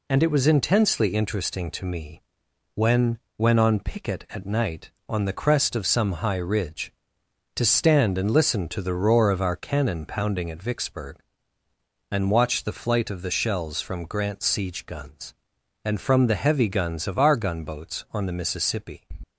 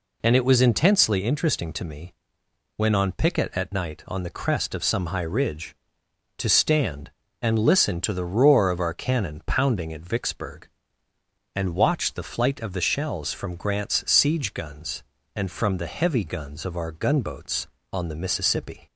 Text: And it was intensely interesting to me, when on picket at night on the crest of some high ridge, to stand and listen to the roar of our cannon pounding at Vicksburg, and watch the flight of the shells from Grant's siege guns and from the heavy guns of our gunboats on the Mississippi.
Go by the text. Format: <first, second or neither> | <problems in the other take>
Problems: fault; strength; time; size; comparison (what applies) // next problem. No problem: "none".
second | says "when" twice; at 3.3 s